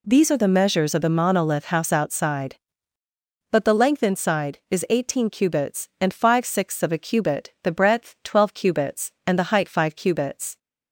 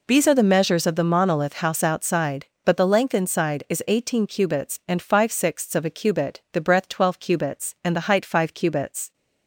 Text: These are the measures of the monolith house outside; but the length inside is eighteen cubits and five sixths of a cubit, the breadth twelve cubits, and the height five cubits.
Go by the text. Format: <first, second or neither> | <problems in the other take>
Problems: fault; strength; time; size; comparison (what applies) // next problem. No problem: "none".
neither | none